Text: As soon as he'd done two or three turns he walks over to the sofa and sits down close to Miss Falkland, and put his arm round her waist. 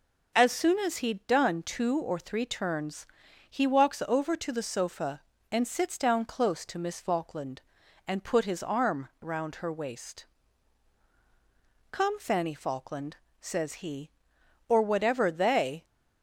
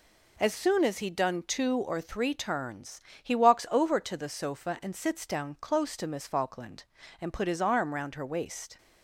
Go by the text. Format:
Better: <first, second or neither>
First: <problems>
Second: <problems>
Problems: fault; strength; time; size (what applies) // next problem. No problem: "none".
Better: second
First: pauses between "turns" and "he"; at 3.0 s; 0.42 s long // goes on to say "Come Fanny Falkland says he or whatever they"; strong; from 11.9 s on; 3.9 s long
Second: pauses between "turns" and "he"; slight; at 3.0 s; 0.22 s long